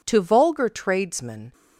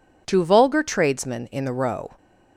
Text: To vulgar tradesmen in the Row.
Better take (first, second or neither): second